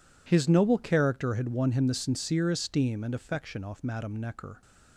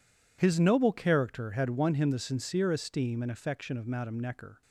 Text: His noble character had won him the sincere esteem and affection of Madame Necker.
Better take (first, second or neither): second